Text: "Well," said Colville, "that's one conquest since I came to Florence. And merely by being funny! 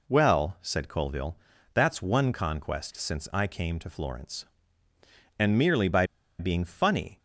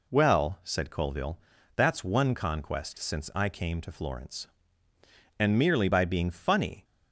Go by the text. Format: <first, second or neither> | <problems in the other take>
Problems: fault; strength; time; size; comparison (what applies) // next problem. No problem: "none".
second | pauses between "by" and "being"; slight; at 6.0 s; 0.33 s long